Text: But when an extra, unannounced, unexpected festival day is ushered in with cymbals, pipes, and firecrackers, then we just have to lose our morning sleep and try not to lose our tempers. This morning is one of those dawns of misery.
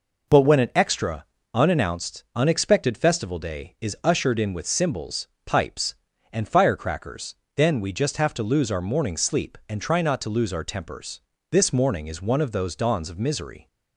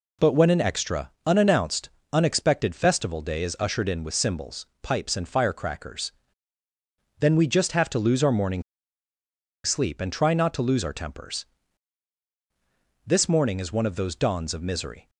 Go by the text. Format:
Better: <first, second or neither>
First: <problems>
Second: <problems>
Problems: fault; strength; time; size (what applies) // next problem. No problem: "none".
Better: first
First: none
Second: pauses between "morning" and "sleep"; at 8.6 s; 1.0 s long